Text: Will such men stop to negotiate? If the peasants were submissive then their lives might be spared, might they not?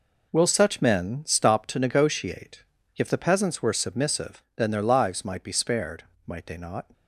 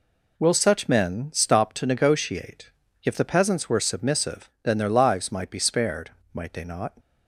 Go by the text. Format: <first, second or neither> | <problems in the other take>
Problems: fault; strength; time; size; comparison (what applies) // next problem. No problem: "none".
second | gets quieter; strong; throughout; 10.5 dB